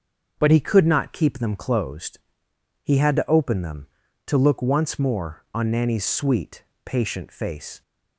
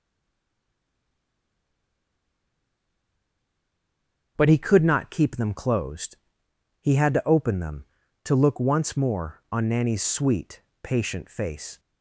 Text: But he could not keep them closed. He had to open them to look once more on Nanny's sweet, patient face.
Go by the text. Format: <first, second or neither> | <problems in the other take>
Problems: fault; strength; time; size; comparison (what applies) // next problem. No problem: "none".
first | stays silent before the first word; strong; until 4.3 s; 4.3 s long // starts louder than the rest; until 5.3 s; 6.5 dB; also in the first